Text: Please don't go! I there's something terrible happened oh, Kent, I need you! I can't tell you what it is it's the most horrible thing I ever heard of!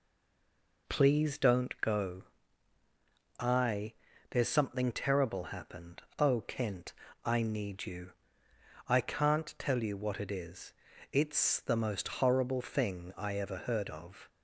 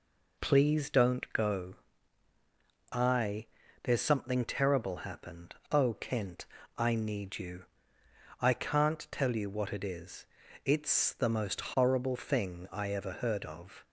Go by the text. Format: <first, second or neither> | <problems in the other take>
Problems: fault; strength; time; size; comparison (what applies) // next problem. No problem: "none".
second | stays silent before the first word; slight; until 0.8 s; 0.8 s long // pauses between "I" and "there's"; slight; at 3.9 s; 0.36 s long; slight in the second // pauses between "happened" and "oh"; slight; at 6.0 s; 0.16 s long; slight in the second // pauses between "is" and "it's"; slight; at 10.7 s; 0.36 s long; slight in the second